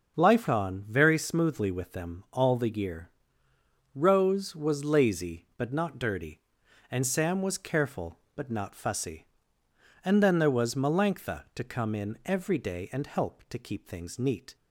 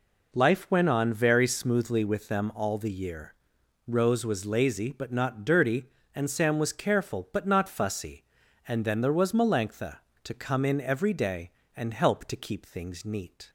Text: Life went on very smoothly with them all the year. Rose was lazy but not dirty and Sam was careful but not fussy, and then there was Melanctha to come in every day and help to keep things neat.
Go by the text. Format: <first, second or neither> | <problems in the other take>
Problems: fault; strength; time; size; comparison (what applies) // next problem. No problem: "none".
second | starts louder than the rest; until 1.2 s; 6.5 dB // skips "went"; at 0.4 s